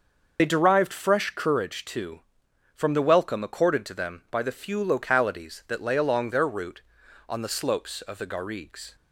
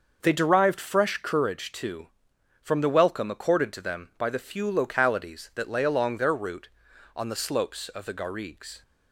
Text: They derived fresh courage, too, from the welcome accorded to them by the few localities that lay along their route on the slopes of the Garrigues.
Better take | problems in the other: second | loses the start of "They"; at 0.3 s; 50 ms // starts louder than the rest; noticeable; until 1.4 s; 6 dB; noticeable in the second

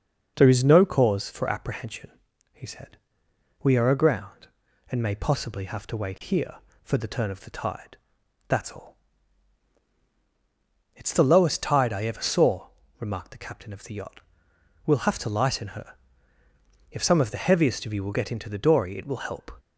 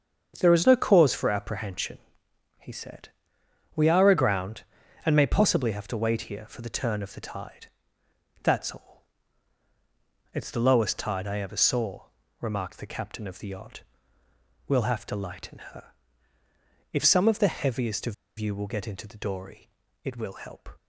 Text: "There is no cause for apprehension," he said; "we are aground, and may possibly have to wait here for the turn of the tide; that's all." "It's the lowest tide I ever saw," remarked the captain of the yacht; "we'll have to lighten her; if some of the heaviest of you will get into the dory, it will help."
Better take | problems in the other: first | starts louder than the rest; strong; until 1.4 s; 7 dB // pauses between "of" and "you"; slight; at 18.1 s; 0.24 s long

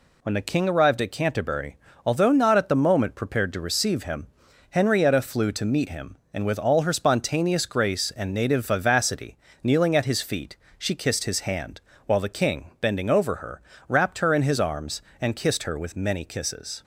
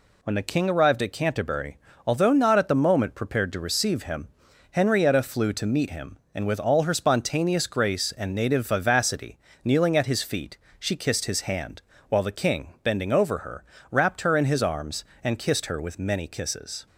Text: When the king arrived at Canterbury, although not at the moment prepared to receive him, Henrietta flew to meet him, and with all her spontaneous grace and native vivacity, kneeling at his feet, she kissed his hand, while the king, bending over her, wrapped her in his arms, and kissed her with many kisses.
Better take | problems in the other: neither | none

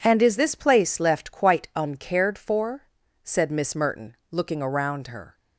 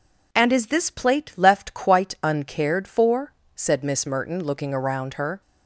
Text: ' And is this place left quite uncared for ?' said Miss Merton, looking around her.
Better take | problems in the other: first | says "plate" for "place"; at 0.9 s

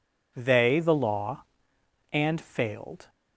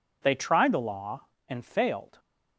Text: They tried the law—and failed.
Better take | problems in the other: second | skips "tried"; at 0.7 s

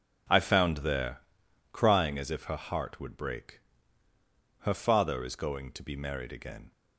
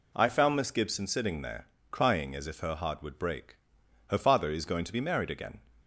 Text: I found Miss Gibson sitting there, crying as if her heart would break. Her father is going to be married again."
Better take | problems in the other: second | skips "Miss Gibson sitting"; at 0.7 s

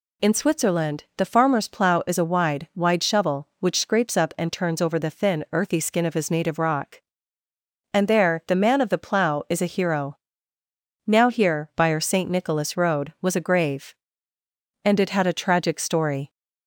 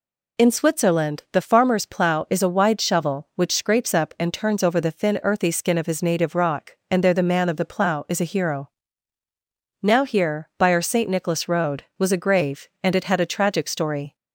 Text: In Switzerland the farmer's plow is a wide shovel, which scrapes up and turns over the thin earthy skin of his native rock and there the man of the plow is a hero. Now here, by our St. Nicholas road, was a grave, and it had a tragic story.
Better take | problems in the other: second | says "wide" twice; at 2.7 s

